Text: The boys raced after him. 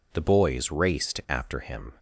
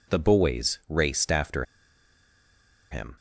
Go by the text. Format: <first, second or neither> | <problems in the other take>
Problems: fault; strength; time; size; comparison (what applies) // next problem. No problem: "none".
first | pauses between "after" and "him"; strong; at 1.6 s; 1.2 s long